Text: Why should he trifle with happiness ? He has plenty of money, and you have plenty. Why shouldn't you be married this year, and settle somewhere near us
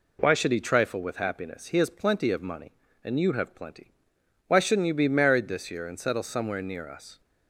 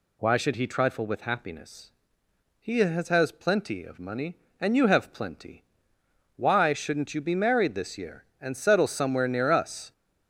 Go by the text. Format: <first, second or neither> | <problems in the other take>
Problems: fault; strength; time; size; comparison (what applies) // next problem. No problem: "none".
first | says "has" twice; at 3.0 s